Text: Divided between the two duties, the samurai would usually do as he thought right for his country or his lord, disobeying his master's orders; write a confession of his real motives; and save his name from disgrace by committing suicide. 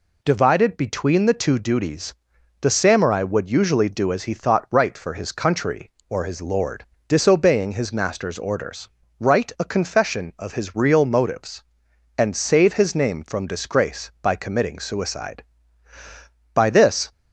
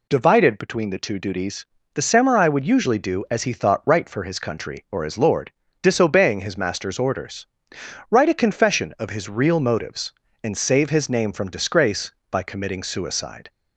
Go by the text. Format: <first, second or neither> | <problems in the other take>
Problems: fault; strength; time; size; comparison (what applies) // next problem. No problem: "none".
second | goes on to say "By this"; from 16.5 s on; 0.58 s long